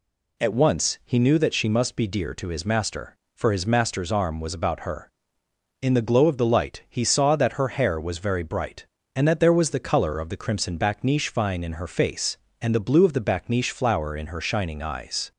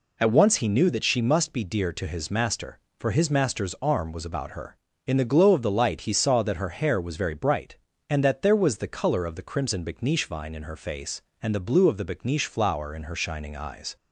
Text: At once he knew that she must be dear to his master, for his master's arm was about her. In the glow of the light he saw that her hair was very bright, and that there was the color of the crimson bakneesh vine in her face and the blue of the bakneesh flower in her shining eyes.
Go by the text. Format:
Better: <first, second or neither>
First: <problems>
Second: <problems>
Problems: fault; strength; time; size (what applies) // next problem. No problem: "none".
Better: neither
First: none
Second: none